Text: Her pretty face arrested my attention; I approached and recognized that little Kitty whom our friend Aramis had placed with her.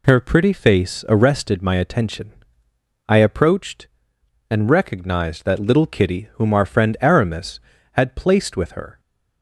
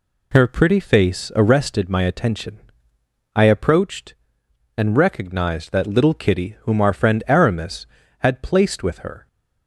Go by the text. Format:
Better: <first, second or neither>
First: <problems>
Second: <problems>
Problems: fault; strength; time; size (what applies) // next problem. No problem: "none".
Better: neither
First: none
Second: none